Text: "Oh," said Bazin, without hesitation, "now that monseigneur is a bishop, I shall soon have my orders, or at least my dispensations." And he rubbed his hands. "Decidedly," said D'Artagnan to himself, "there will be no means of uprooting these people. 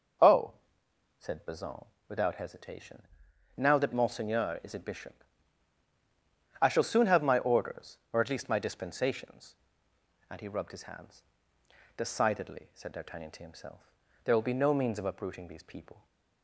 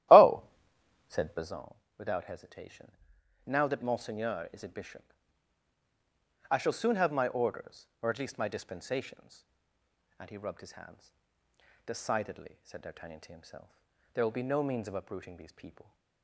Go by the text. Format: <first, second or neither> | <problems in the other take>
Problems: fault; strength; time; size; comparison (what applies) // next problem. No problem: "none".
first | starts louder than the rest; strong; until 1.6 s; 13.5 dB